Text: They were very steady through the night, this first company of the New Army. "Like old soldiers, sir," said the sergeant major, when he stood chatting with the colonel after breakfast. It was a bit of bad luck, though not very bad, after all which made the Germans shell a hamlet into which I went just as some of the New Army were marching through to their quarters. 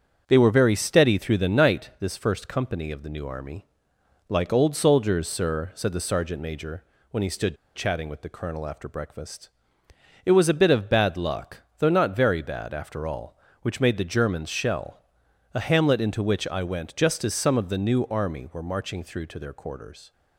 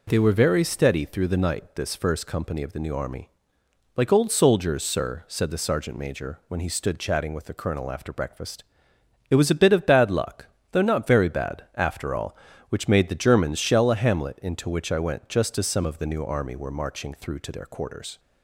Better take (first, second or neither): second